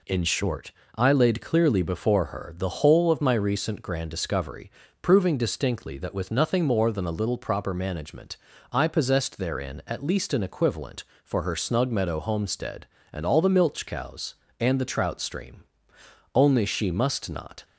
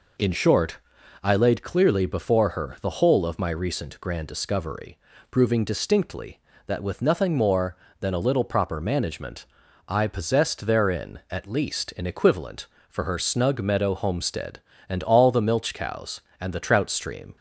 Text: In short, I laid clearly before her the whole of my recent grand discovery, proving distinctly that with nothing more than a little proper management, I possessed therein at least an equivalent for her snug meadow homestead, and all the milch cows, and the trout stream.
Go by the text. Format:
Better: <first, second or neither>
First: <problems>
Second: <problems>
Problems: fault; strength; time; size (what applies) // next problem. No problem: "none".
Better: second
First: goes on to say "Only she must not"; noticeable; from 16.3 s on; 1.3 s long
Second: none